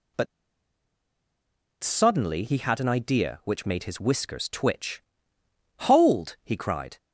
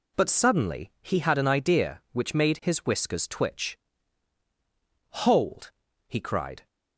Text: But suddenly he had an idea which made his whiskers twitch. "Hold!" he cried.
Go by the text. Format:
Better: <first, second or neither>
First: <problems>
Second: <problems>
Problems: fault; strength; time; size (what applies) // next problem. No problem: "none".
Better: second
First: pauses between "But" and "suddenly"; strong; at 0.2 s; 1.5 s long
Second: none